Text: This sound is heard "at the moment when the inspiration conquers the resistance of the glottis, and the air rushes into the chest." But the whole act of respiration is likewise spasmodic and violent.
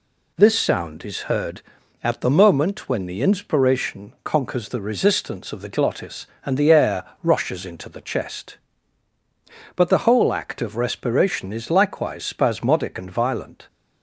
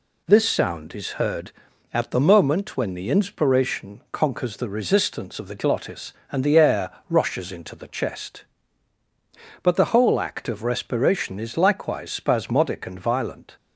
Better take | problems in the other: neither | pauses between "air" and "rushes"; slight; the same in both

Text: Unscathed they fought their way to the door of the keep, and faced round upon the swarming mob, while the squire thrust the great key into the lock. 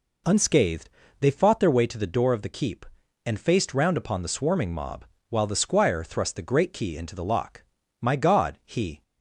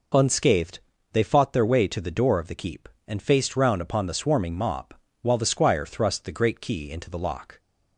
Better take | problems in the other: second | pauses between "Unscathed" and "they"; slight; at 0.8 s; 0.32 s long; slight in the second // goes on to say "My God he"; noticeable; from 7.9 s on; 1.0 s long

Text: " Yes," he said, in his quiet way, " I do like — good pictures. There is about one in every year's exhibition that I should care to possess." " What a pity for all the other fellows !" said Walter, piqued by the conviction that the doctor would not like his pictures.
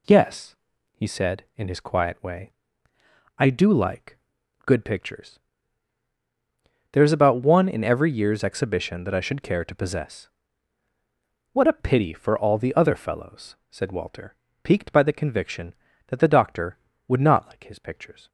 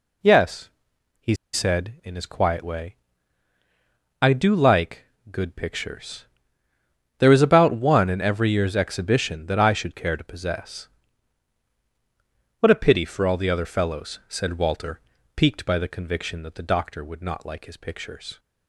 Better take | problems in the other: first | pauses between "he" and "said"; slight; at 1.3 s; 0.19 s long

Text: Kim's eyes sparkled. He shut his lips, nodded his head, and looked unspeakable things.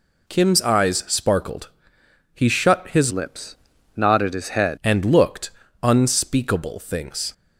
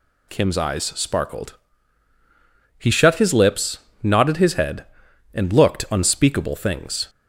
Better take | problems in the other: second | changes voice from "lips" to "head"; from 3.1 to 4.7 s; 1.6 s long // pauses between "looked" and "unspeakable"; slight; at 5.5 s; 0.30 s long

